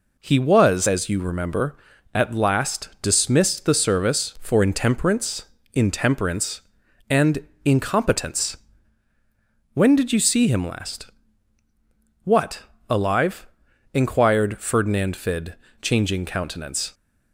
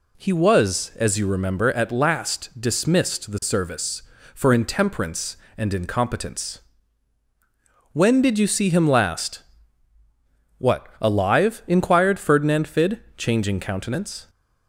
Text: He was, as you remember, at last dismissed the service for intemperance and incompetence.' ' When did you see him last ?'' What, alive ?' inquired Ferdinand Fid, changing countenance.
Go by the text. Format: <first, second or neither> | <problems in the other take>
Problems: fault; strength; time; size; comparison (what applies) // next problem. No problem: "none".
second | says "intemperance" twice; at 5.7 s // pauses between "and" and "incompetence"; slight; at 7.3 s; 0.26 s long